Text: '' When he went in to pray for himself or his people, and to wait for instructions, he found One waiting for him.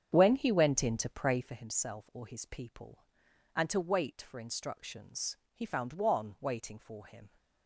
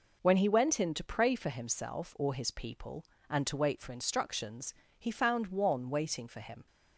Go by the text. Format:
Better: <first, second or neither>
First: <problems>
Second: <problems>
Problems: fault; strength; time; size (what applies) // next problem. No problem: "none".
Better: second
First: starts louder than the rest; strong; until 1.5 s; 8.5 dB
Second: none